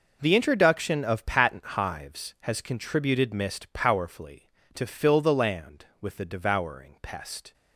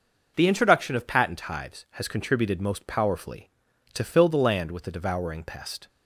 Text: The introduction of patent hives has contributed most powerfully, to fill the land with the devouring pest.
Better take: second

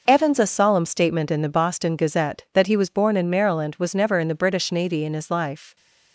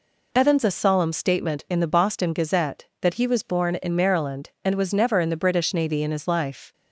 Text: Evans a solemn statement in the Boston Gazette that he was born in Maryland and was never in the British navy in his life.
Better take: second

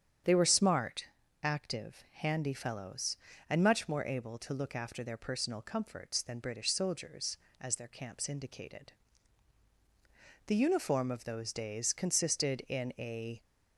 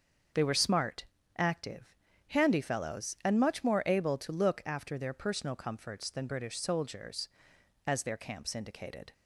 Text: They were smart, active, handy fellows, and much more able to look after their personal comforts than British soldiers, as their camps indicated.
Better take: second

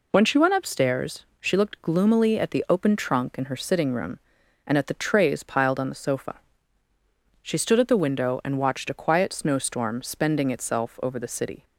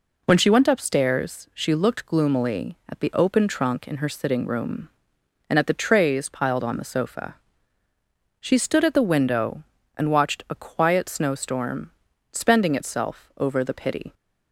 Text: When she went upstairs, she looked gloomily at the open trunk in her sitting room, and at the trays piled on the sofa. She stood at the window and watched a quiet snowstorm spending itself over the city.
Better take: first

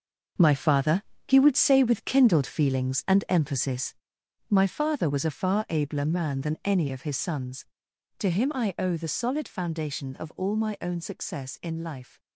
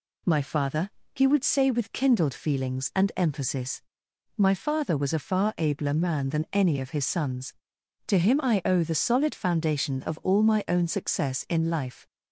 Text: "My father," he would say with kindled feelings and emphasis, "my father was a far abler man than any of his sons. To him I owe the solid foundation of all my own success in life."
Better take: second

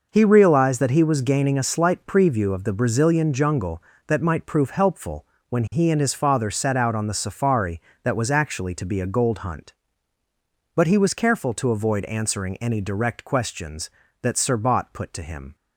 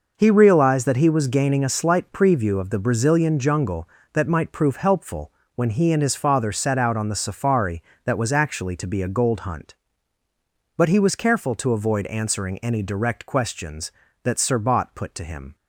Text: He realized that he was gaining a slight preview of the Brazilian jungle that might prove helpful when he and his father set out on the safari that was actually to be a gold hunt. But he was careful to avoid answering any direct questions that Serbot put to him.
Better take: neither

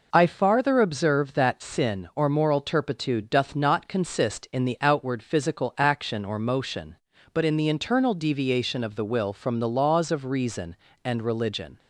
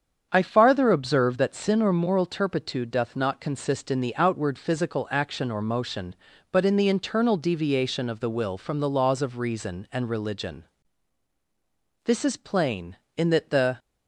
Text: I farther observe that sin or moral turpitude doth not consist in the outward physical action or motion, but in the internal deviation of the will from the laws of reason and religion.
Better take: first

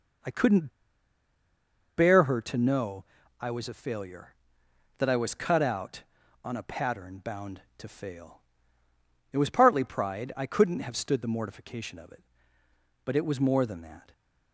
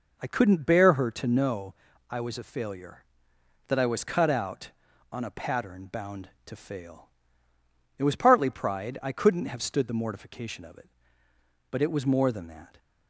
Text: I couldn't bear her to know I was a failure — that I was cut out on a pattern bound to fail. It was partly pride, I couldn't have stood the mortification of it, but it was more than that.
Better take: second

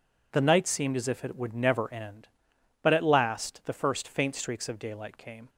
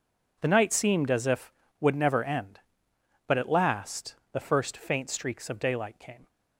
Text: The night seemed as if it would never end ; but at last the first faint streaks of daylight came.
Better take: first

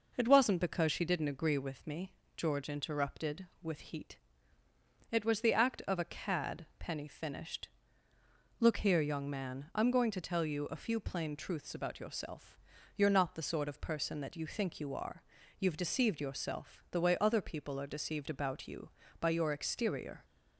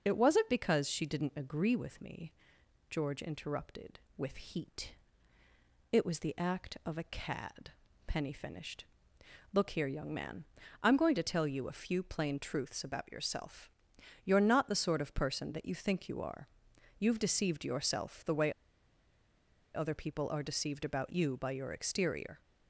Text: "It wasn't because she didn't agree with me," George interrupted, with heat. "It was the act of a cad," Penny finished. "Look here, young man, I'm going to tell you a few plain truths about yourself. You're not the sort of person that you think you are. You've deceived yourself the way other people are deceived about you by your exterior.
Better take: first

